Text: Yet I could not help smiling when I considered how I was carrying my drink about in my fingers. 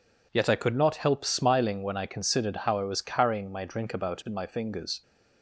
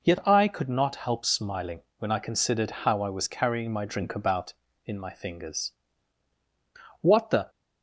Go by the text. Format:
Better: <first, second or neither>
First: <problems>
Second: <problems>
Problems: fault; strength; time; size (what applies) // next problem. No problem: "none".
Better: first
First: none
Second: pauses between "smiling" and "when"; slight; at 1.8 s; 0.16 s long // goes on to say "What the"; slight; from 7.0 s on; 0.48 s long